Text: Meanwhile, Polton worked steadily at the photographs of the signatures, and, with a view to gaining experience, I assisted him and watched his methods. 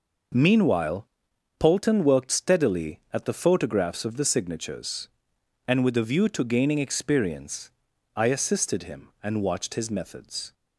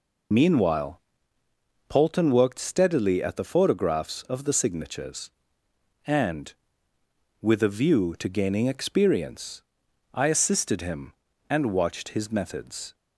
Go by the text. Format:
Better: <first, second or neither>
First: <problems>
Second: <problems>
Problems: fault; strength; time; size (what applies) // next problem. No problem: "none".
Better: first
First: none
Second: loses the start of "Meanwhile"; at 0.3 s; 65 ms